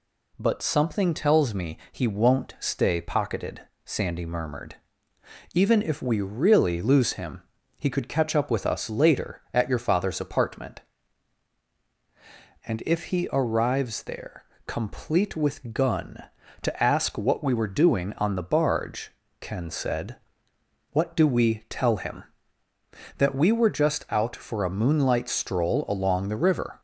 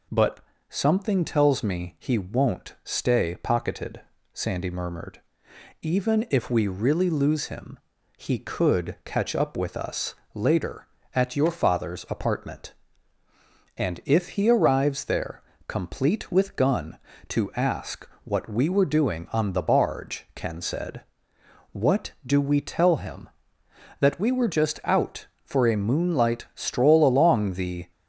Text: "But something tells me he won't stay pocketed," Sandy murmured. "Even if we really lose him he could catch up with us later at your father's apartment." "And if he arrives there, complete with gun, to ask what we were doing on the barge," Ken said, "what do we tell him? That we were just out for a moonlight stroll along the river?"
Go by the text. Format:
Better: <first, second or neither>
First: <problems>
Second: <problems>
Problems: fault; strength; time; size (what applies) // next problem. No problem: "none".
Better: first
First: pauses between "him" and "he"; slight; at 7.4 s; 0.36 s long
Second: pauses between "But" and "something"; slight; at 0.4 s; 0.28 s long // pauses between "him" and "he"; at 7.7 s; 0.38 s long // pauses between "us" and "later"; slight; at 10.1 s; 0.18 s long // pauses between "ask" and "what"; slight; at 18.0 s; 0.16 s long // stops before "river"; at 27.9 s